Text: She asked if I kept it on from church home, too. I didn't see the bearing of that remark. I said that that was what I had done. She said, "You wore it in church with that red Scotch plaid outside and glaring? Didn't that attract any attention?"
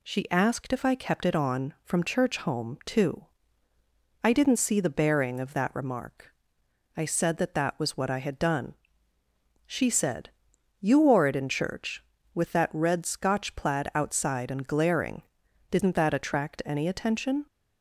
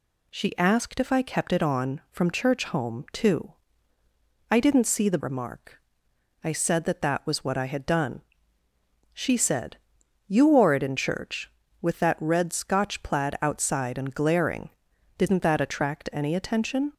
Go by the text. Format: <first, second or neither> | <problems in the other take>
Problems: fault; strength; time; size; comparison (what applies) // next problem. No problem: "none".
first | skips "bearing of that"; at 5.1 s